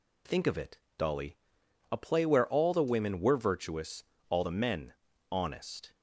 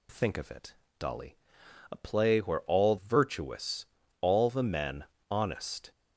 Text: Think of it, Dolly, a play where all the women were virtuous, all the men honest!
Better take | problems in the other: first | skips "the women were"; at 2.9 s // pauses between "men" and "honest"; slight; at 5.0 s; 0.26 s long; slight in the first

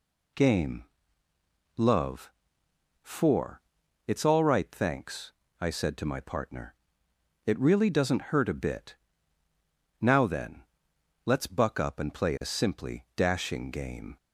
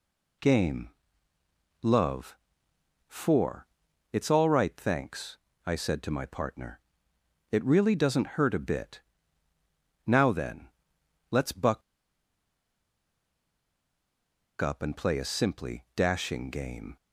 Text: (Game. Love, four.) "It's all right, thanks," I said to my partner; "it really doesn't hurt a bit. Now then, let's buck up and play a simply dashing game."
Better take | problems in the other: first | pauses between "buck" and "up"; strong; at 11.8 s; 2.8 s long

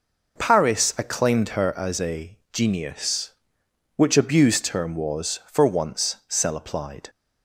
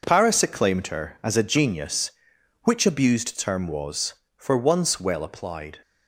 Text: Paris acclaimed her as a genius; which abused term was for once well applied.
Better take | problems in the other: second | pauses between "a" and "genius"; slight; at 2.3 s; 0.16 s long // says "cell" for "well"; at 6.2 s

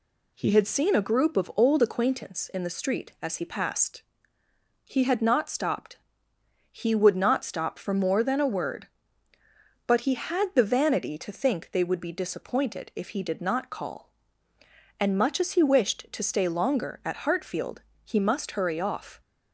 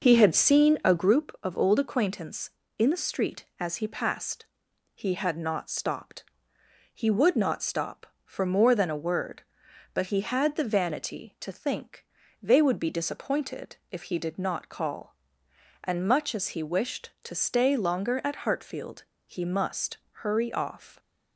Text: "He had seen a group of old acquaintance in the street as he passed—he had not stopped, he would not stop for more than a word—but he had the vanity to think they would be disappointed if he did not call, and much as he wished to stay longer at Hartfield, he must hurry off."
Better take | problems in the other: first | starts louder than the rest; noticeable; until 1.3 s; 5.5 dB // pauses between "think" and "they"; at 12.0 s; 0.38 s long // pauses between "disappointed" and "if"; slight; at 13.7 s; 0.16 s long // pauses between "must" and "hurry"; slight; at 19.9 s; 0.16 s long

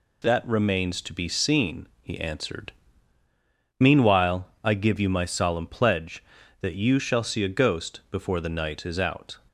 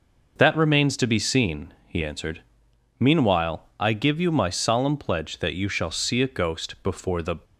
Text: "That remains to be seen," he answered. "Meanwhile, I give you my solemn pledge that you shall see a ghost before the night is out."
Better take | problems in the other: first | stops before "night is out"; at 7.4 s

